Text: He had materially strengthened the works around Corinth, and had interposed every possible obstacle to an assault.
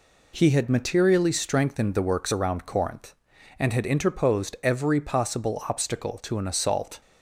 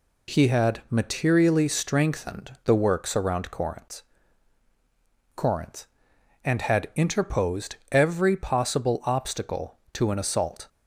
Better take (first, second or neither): first